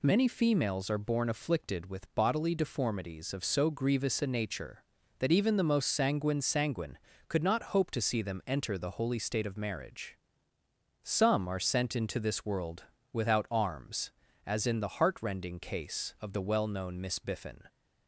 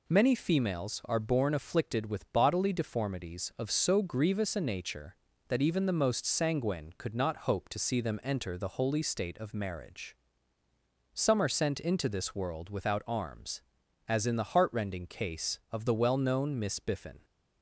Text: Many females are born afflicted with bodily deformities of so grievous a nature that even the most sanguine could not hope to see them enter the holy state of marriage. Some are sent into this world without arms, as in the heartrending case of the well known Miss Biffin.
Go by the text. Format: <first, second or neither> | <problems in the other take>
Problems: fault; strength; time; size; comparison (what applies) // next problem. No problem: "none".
second | says "sanguine" twice; at 6.4 s // pauses between "world" and "without"; slight; at 12.8 s; 0.28 s long